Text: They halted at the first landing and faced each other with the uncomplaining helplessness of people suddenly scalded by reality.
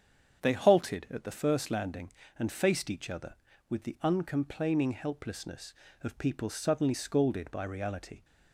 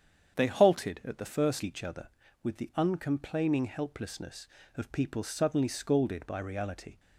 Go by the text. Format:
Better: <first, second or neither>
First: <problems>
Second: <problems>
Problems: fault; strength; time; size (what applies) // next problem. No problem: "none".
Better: first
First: starts louder than the rest; strong; until 1.4 s; 8 dB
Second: starts louder than the rest; strong; until 1.4 s; 8 dB // skips "landing and faced"; at 1.6 s